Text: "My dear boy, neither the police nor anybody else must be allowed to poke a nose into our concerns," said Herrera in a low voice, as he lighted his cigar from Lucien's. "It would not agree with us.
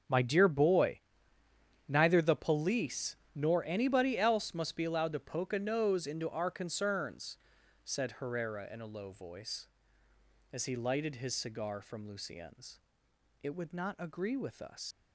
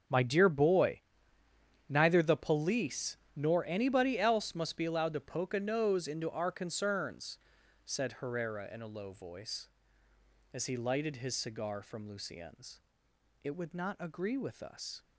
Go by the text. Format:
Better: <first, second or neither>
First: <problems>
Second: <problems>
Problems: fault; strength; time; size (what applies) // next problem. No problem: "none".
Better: second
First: starts louder than the rest; until 1.9 s; 6.5 dB // pauses between "police" and "nor"; slight; at 3.1 s; 0.18 s long // leaves "us" unfinished; at 14.9 s; 100 ms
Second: starts louder than the rest; until 1.9 s; 6.5 dB // pauses between "police" and "nor"; slight; at 3.1 s; 0.18 s long